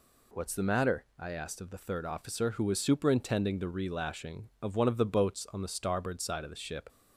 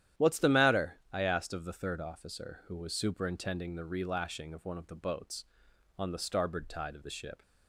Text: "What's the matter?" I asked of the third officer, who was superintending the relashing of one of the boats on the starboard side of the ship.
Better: first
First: none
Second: starts louder than the rest; strong; until 1.2 s; 11 dB // says "tide" for "side"; at 6.6 s

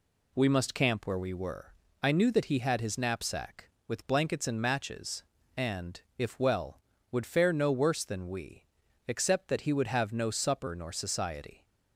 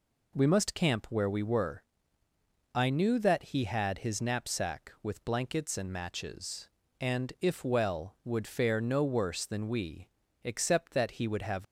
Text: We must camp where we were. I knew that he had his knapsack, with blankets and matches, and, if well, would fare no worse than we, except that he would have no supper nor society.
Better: first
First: none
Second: stops before "no supper nor society"; at 11.6 s

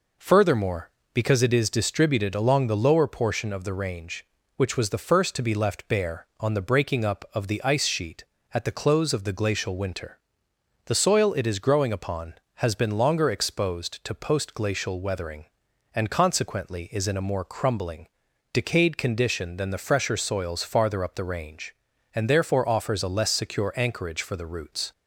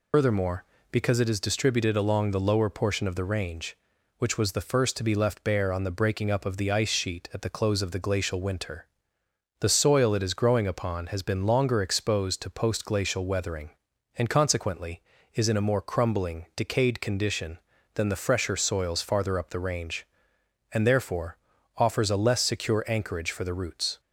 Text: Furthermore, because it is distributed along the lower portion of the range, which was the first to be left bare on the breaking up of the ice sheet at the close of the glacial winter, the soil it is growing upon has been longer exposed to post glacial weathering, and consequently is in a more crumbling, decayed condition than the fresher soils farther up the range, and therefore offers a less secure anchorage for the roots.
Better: first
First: none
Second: loses the start of "Furthermore"; at 0.1 s; 120 ms // pauses between "therefore" and "offers"; at 21.3 s; 0.40 s long

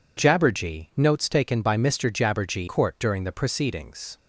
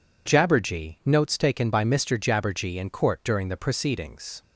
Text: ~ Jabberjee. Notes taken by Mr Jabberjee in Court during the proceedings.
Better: second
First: skips "in"; at 2.6 s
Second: none

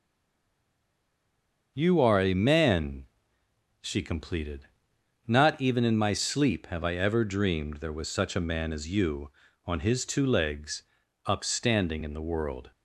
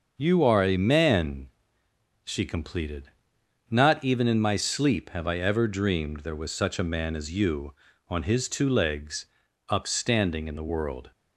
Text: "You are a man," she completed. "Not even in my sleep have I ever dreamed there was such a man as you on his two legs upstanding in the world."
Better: second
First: stays silent before the first word; noticeable; until 1.7 s; 1.7 s long // starts louder than the rest; until 2.7 s; 6.5 dB // pauses between "legs" and "upstanding"; noticeable; at 10.8 s; 0.46 s long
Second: starts louder than the rest; until 1.1 s; 6.5 dB // pauses between "legs" and "upstanding"; noticeable; at 9.2 s; 0.46 s long

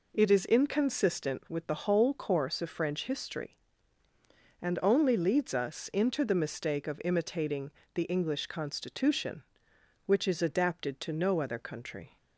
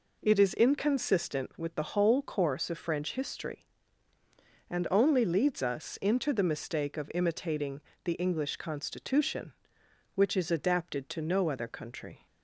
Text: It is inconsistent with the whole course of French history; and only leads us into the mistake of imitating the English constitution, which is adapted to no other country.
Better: neither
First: pauses between "imitating" and "the"; slight; at 7.7 s; 0.22 s long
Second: pauses between "imitating" and "the"; slight; at 7.8 s; 0.22 s long

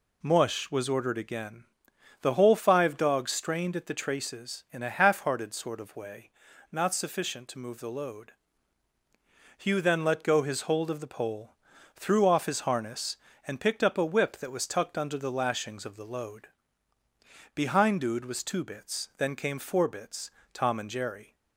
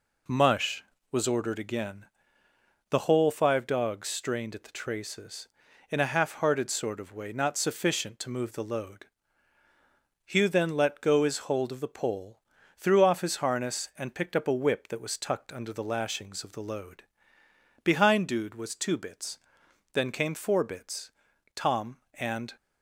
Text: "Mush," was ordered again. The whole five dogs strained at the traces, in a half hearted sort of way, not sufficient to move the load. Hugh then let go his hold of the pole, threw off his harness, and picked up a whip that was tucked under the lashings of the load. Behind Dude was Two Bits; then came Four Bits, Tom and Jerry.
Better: first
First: none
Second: stops before "Jerry"; at 22.5 s

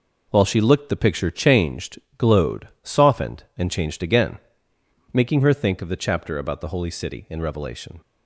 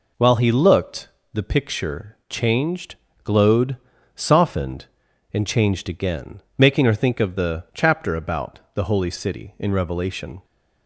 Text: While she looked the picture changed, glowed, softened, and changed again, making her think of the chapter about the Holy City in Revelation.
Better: first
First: none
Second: says "he" for "she"; at 0.3 s // pauses between "looked" and "the"; slight; at 1.0 s; 0.24 s long

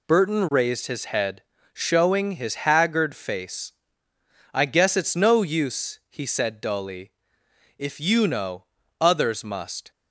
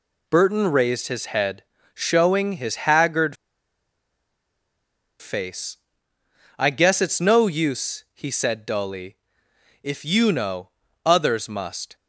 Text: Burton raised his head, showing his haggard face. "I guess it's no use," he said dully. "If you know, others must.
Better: first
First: none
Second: pauses between "haggard" and "face"; strong; at 3.3 s; 1.8 s long

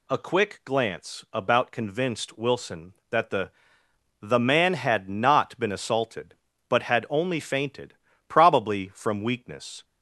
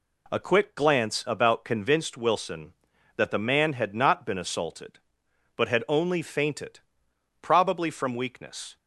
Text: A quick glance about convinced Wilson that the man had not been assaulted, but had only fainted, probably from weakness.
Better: second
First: says "the" twice; at 4.2 s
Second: none

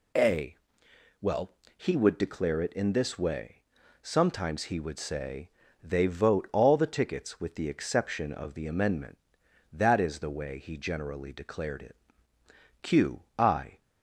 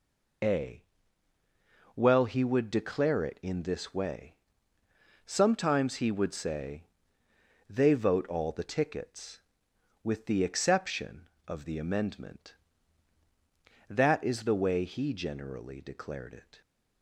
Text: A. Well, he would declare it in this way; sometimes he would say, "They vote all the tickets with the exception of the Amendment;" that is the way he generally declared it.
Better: second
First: goes on to say "Q I"; noticeable; from 12.8 s on; 1.0 s long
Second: none

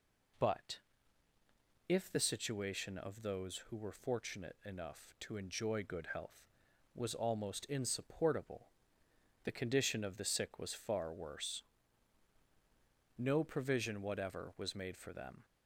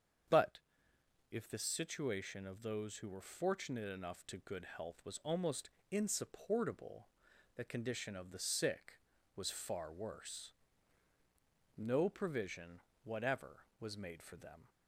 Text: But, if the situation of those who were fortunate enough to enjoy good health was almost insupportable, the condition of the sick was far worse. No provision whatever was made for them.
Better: first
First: none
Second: starts louder than the rest; strong; until 2.0 s; 7 dB // skips "enjoy"; at 4.3 s // pauses between "almost" and "insupportable"; slight; at 5.6 s; 0.22 s long // pauses between "provision" and "whatever"; slight; at 12.8 s; 0.22 s long

